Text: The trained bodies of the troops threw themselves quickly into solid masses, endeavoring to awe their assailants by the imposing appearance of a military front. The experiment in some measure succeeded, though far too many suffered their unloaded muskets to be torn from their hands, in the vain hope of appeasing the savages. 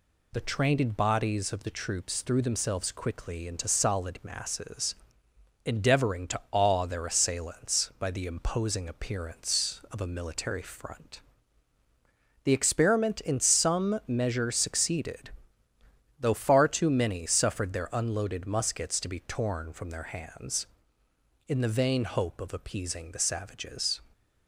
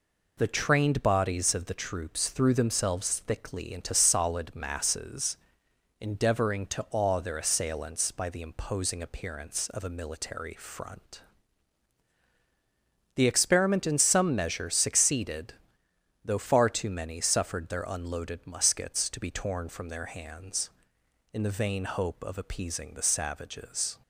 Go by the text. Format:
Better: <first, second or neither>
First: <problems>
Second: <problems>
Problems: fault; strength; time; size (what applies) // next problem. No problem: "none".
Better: first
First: none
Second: says "thickly" for "quickly"; at 3.2 s